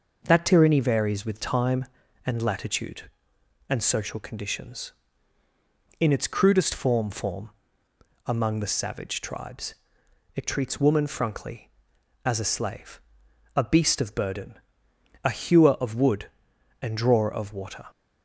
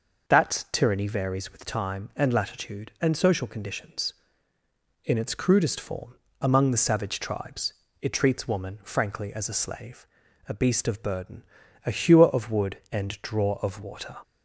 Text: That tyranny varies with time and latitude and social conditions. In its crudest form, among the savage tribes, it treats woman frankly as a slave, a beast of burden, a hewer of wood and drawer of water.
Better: second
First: says "form" twice; at 7.0 s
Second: none

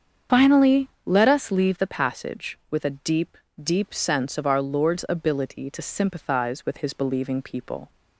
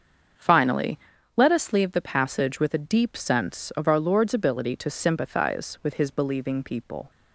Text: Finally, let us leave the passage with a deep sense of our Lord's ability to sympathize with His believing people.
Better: second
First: starts louder than the rest; strong; until 1.4 s; 7.5 dB // says "deep" twice; at 3.6 s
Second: starts louder than the rest; until 1.7 s; 6.5 dB

